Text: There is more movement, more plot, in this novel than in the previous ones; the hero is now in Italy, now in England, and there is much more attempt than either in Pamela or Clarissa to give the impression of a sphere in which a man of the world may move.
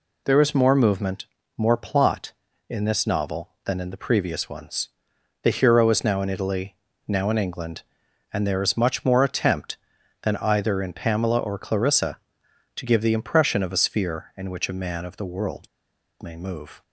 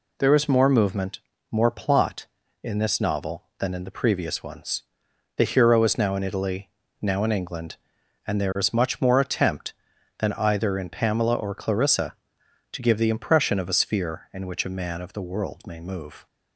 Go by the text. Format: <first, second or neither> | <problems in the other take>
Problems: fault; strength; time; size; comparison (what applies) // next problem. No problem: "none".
second | pauses between "world" and "may"; noticeable; at 15.6 s; 0.53 s long